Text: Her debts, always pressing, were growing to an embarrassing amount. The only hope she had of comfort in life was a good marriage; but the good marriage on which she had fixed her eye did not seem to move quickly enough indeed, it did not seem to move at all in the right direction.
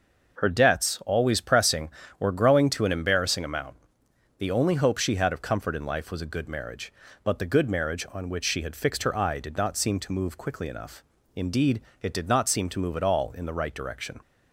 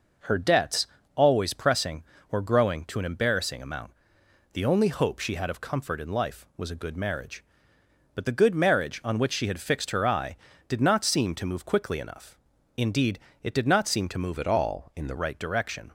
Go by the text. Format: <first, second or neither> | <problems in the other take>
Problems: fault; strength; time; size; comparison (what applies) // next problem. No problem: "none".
first | pauses between "enough" and "indeed"; at 12.3 s; 0.38 s long; slight in the first // changes voice from "at" to "the"; from 14.3 to 15.1 s; 0.8 s long